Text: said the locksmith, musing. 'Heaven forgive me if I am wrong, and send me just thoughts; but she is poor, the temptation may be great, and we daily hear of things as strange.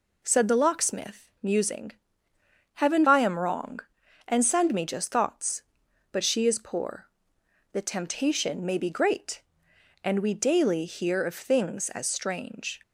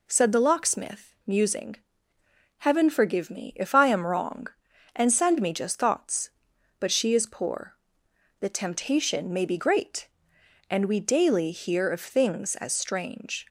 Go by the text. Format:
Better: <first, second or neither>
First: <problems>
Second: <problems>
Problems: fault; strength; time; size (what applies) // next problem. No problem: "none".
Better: second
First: skips "forgive me if"; at 3.0 s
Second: none